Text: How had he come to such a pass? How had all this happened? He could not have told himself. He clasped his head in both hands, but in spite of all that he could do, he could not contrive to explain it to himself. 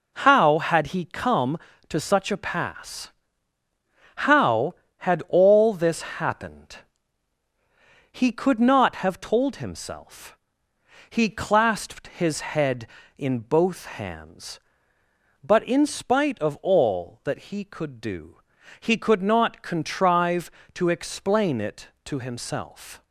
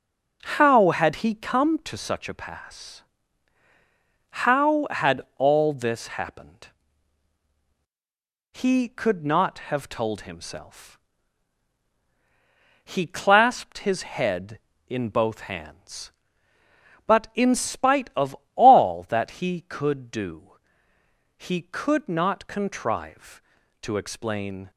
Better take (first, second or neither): first